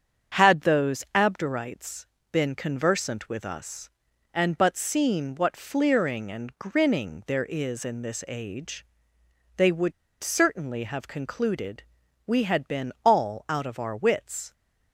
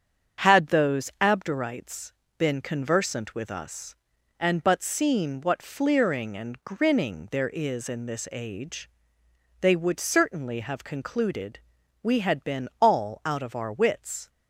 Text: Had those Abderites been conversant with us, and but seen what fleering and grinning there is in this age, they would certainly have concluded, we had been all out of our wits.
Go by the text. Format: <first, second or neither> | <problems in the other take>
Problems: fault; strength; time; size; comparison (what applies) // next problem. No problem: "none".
second | starts louder than the rest; strong; until 1.4 s; 7.5 dB; strong in the second // pauses between "Abderites" and "been"; slight; at 2.0 s; 0.24 s long; slight in the second // pauses between "would" and "certainly"; slight; at 9.9 s; 0.29 s long